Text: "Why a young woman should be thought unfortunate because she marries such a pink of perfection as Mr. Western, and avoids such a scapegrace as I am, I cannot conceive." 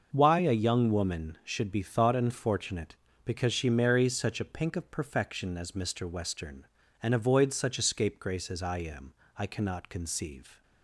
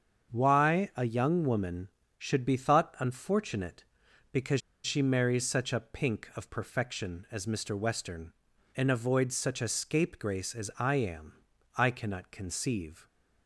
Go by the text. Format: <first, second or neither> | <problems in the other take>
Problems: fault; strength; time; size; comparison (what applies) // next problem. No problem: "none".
first | starts louder than the rest; strong; until 1.3 s; 7 dB; also in the first // pauses between "because" and "she"; slight; at 4.6 s; 0.24 s long